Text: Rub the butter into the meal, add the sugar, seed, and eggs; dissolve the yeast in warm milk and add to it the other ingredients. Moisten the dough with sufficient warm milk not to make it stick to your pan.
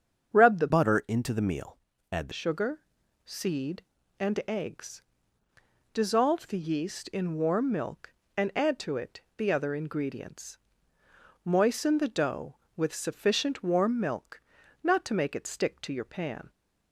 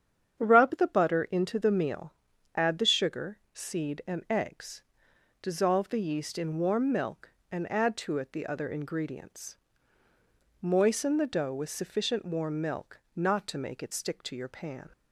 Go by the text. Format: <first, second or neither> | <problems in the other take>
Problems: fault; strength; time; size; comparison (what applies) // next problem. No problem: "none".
second | starts louder than the rest; strong; until 1.4 s; 7.5 dB; strong in the second // changes voice from "butter" to "the"; from 0.6 to 2.3 s; 1.7 s long // pauses between "it" and "the"; slight; at 9.2 s; 0.16 s long // pauses between "milk" and "not"; at 14.4 s; 0.42 s long; slight in the second